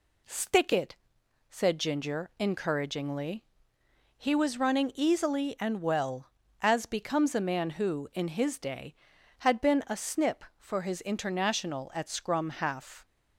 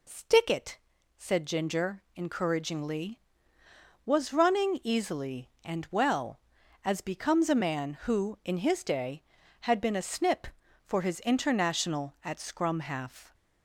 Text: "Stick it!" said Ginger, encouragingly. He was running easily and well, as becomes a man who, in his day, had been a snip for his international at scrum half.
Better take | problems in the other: first | skips "He"; at 3.6 s

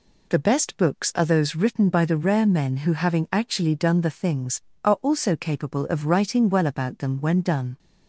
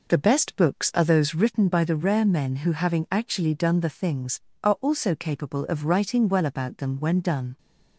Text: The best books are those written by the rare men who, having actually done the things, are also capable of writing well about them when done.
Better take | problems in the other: first | starts louder than the rest; noticeable; until 1.6 s; 4.5 dB

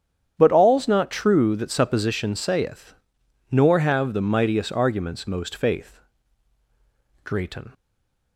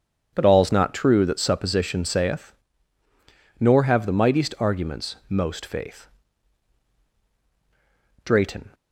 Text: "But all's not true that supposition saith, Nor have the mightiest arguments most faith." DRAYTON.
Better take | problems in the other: second | starts louder than the rest; strong; until 1.3 s; 9 dB // stays silent after the last word; slight; from 7.7 s on; 0.6 s long

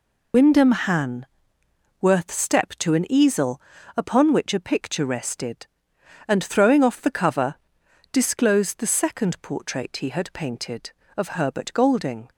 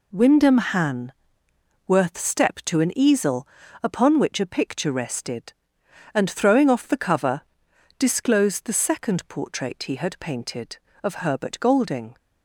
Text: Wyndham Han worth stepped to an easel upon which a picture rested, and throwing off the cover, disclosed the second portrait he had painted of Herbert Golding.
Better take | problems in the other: second | loses the start of "Wyndham"; at 0.3 s; 85 ms // pauses between "Han" and "worth"; noticeable; at 1.2 s; 0.74 s long; noticeable in the second // pauses between "easel" and "upon"; slight; at 3.6 s; 0.34 s long; slight in the second

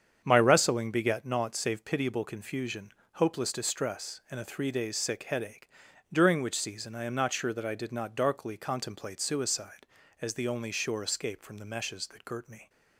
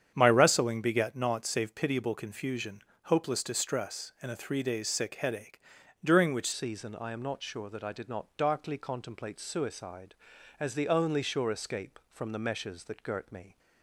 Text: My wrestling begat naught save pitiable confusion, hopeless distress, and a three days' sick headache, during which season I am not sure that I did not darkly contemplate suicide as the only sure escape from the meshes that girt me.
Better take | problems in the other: first | starts louder than the rest; strong; until 1.1 s; 8.5 dB; strong in the first // changes voice at "season"; from 6.5 s on; 7.0 s long

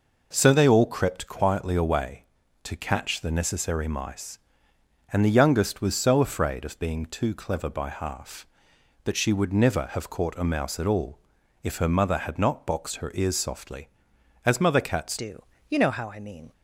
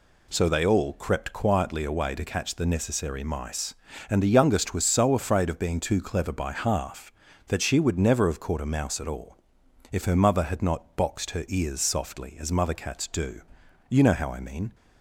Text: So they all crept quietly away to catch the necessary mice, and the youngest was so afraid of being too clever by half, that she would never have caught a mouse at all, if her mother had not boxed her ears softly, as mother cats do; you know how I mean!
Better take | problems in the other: second | changes voice at "do"; from 15.1 s on; 1.4 s long

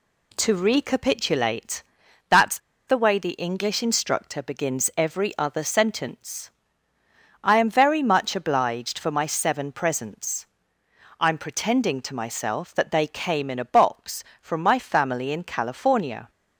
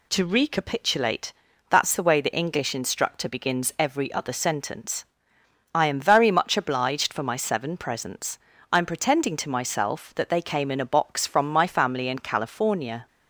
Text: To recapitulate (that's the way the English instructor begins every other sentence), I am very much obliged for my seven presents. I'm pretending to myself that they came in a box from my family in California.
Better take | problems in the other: second | pauses between "that's" and "the"; slight; at 2.5 s; 0.29 s long

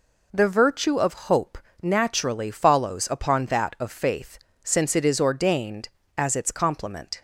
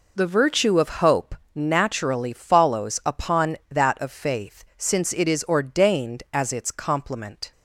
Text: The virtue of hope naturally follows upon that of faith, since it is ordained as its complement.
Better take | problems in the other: neither | pauses between "hope" and "naturally"; slight; the same in both

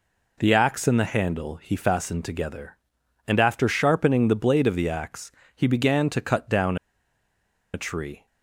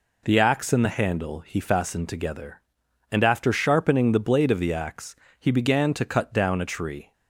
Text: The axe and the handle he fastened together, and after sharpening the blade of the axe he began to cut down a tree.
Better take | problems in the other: second | pauses between "axe" and "he"; slight; at 5.3 s; 0.24 s long; slight in the second // pauses between "down" and "a"; noticeable; at 6.7 s; 0.96 s long

